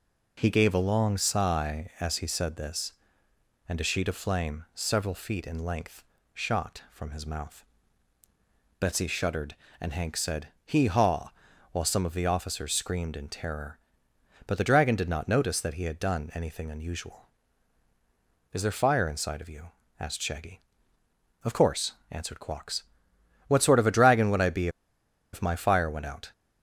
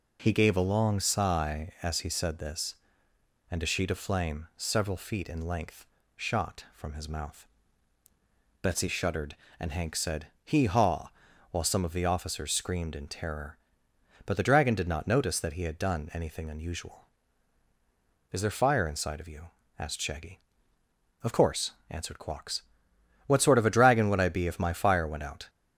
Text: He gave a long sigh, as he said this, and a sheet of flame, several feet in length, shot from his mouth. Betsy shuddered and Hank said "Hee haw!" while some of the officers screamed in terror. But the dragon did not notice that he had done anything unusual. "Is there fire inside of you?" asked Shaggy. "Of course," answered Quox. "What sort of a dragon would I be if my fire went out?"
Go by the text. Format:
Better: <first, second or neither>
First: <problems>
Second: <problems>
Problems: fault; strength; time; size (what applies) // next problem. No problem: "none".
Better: second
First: pauses between "be" and "if"; noticeable; at 24.6 s; 0.64 s long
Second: none